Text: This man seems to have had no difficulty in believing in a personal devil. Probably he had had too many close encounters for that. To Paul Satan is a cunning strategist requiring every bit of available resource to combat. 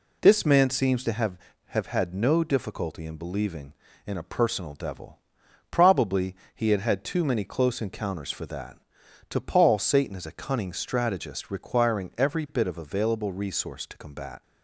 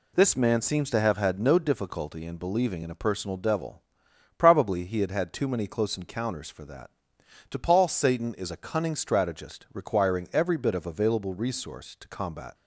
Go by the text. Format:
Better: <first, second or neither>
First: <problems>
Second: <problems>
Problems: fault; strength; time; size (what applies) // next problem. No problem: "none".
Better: second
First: says "have" twice; at 1.6 s // pauses between "Probably" and "he"; slight; at 6.3 s; 0.18 s long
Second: none